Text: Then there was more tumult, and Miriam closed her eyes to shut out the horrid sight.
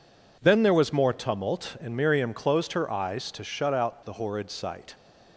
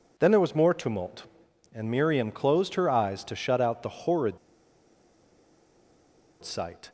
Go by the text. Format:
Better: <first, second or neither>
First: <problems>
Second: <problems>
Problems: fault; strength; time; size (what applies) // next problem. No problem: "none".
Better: first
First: none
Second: pauses between "horrid" and "sight"; strong; at 4.3 s; 2.0 s long